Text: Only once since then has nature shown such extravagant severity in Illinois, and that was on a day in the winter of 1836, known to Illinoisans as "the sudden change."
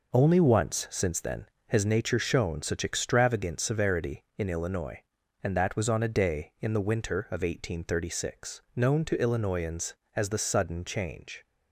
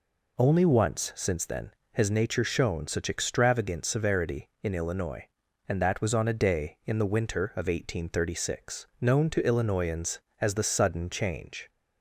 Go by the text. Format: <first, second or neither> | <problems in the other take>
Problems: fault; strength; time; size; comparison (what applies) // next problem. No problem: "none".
second | gets quieter; strong; throughout; 7.5 dB